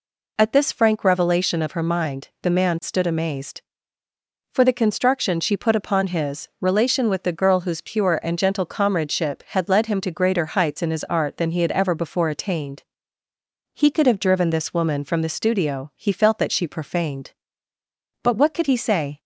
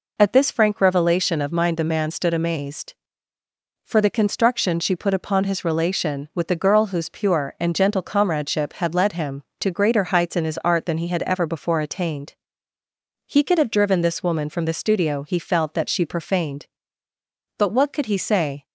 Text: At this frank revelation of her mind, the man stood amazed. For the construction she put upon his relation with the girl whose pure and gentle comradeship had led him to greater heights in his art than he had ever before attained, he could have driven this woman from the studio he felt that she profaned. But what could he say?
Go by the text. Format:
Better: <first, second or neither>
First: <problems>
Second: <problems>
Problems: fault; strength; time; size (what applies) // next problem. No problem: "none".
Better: first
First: none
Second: skips "her"; at 1.5 s